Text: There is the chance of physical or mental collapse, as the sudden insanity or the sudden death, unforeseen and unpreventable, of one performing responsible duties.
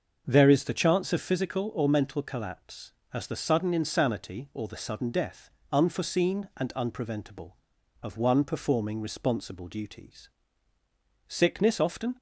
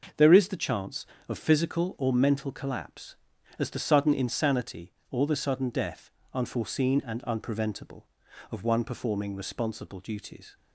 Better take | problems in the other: second | starts louder than the rest; noticeable; until 1.2 s; 6 dB // goes on to say "Sickness often"; noticeable; from 11.2 s on; 0.88 s long

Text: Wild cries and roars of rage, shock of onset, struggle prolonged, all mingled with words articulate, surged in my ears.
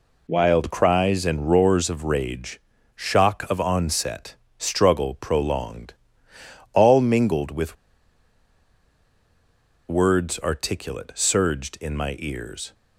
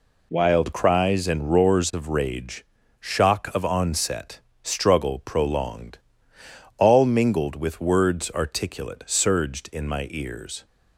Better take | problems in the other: second | pauses between "with" and "words"; strong; at 7.7 s; 2.1 s long

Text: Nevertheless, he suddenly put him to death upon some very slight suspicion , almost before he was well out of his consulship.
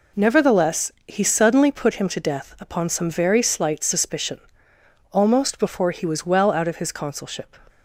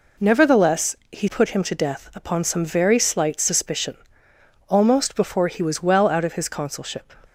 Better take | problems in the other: first | skips "suddenly"; at 1.2 s

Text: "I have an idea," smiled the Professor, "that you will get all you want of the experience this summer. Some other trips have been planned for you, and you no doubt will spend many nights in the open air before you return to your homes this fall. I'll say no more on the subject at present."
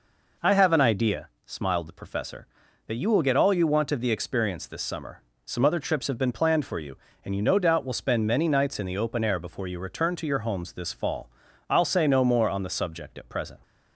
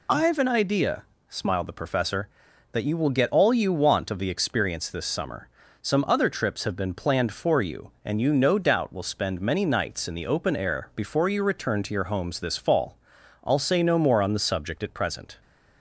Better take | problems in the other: first | loses the start of "I"; at 0.0 s; 50 ms

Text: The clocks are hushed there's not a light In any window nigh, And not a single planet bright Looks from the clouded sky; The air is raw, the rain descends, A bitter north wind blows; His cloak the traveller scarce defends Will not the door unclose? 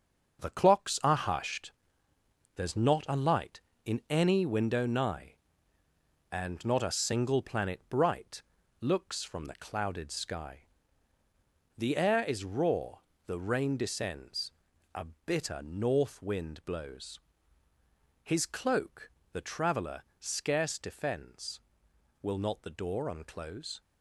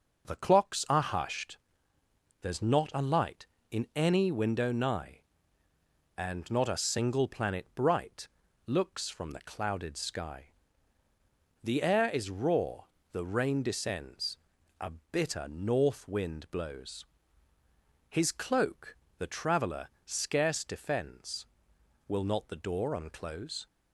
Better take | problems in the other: second | gets quieter; strong; throughout; 7.5 dB // pauses between "hushed" and "there's"; noticeable; at 1.7 s; 0.82 s long; noticeable in the second // pauses between "bright" and "Looks"; at 8.4 s; 0.38 s long; also in the second // pauses between "A" and "bitter"; slight; at 15.0 s; 0.22 s long; slight in the second // pauses between "cloak" and "the"; slight; at 19.1 s; 0.22 s long; slight in the second // pauses between "traveller" and "scarce"; slight; at 20.0 s; 0.18 s long; slight in the second

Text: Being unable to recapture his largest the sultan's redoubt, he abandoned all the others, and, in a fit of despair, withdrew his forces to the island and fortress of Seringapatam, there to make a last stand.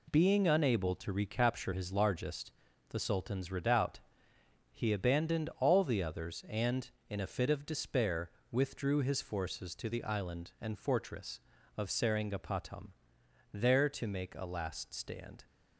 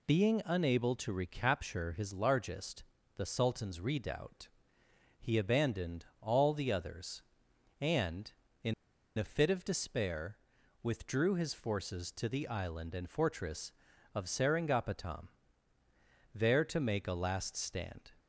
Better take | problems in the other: first | pauses between "largest" and "the"; slight; at 2.8 s; 0.34 s long; also in the first // pauses between "abandoned" and "all"; slight; at 6.0 s; 0.16 s long // pauses between "in" and "a"; at 8.7 s; 0.44 s long

